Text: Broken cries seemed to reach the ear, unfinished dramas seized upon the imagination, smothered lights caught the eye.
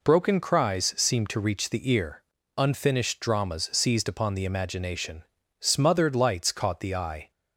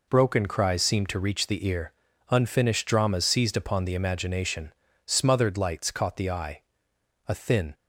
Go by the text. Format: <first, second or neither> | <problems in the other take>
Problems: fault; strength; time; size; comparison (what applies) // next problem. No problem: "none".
first | goes on to say "A thin"; slight; from 7.2 s on; 0.46 s long